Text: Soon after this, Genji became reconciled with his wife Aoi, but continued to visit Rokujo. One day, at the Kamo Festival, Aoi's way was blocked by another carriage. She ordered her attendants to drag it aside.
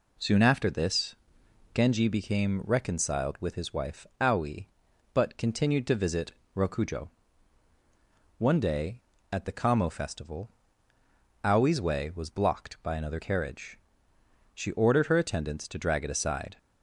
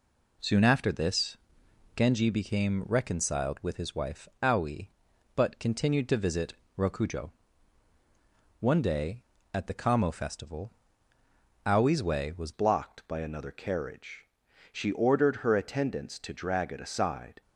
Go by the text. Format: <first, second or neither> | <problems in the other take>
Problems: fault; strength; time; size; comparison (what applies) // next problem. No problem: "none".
first | pauses between "visit" and "Rokujo"; slight; at 6.5 s; 0.24 s long; slight in the first // changes voice at "blocked"; from 12.5 s on; 4.9 s long